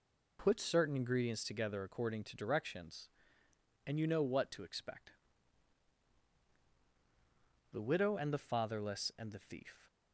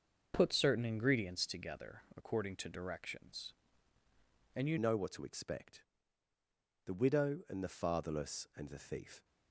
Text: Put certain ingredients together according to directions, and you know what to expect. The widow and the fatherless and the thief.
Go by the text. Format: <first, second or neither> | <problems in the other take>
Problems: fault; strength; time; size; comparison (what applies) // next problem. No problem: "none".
first | starts louder than the rest; noticeable; until 1.3 s; 6 dB // pauses between "together" and "according"; slight; at 2.0 s; 0.16 s long // changes voice at "know"; from 4.7 s on; 4.5 s long